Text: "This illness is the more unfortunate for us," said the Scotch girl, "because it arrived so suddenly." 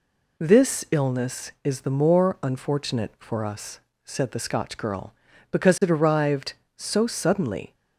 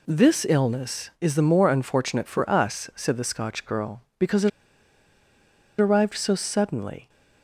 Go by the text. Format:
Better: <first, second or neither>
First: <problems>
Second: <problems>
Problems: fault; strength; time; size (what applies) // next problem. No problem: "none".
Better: first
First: none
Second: pauses between "it" and "arrived"; strong; at 4.4 s; 1.3 s long